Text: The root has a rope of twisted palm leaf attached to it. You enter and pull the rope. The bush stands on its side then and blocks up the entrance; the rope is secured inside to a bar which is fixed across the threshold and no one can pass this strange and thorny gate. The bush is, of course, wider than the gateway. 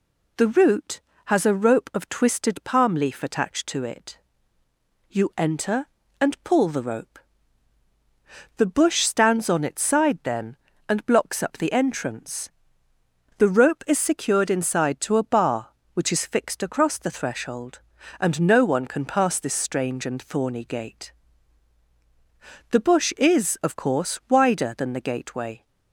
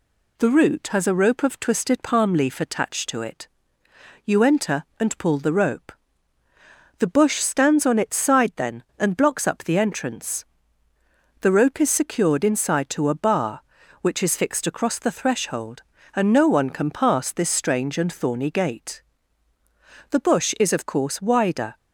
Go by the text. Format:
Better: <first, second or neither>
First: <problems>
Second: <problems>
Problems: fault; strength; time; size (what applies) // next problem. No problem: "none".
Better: first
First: none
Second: stops before "than the gateway"; at 21.7 s